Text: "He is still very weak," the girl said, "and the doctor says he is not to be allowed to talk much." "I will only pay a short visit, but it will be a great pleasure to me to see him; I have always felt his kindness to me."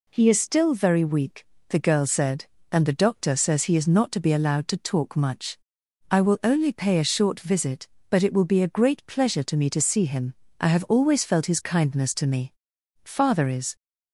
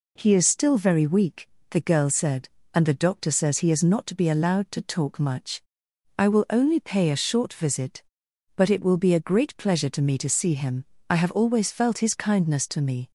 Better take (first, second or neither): second